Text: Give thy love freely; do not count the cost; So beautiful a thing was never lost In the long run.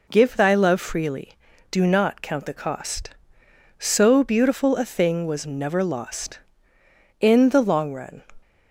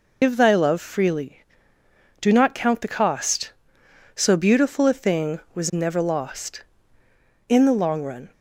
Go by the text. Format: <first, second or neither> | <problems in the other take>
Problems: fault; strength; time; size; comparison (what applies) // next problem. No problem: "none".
first | loses the start of "Give"; at 0.2 s; 110 ms